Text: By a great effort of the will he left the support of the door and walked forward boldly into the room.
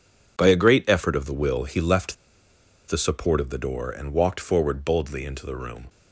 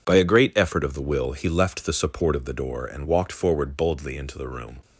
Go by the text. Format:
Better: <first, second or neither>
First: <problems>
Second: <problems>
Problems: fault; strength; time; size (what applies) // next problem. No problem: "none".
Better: second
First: pauses between "left" and "the"; noticeable; at 2.1 s; 0.74 s long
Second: none